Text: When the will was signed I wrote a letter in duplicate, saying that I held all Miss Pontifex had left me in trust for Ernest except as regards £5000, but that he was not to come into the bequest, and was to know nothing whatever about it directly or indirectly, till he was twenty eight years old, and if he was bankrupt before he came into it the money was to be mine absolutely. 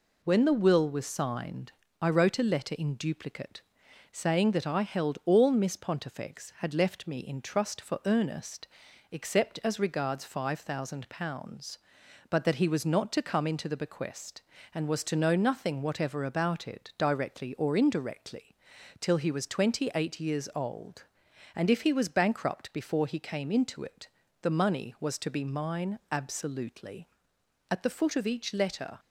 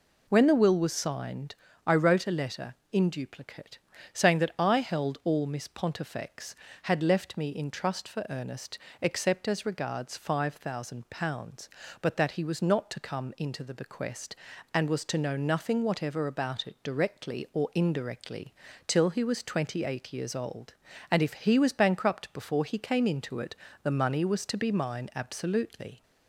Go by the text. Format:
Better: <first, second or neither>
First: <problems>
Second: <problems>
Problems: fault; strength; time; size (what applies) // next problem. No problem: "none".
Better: second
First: pauses between "signed" and "I"; slight; at 1.7 s; 0.26 s long // pauses between "Ernest" and "except"; noticeable; at 8.6 s; 0.46 s long // pauses between "it" and "the"; slight; at 24.0 s; 0.34 s long // goes on to say "At the foot of each letter"; noticeable; from 27.6 s on; 1.3 s long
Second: pauses between "signed" and "I"; slight; at 1.5 s; 0.32 s long // pauses between "Ernest" and "except"; slight; at 8.7 s; 0.24 s long // pauses between "it" and "the"; slight; at 23.5 s; 0.26 s long